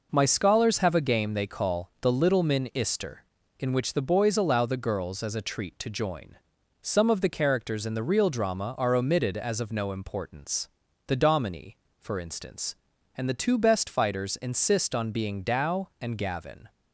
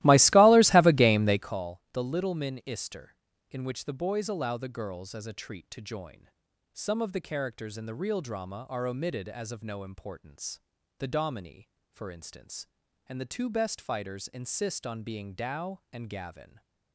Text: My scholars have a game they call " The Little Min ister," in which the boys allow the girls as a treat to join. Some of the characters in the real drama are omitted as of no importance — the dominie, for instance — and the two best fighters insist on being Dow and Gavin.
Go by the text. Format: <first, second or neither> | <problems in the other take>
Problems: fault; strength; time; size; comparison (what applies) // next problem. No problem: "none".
first | starts louder than the rest; strong; until 1.6 s; 17 dB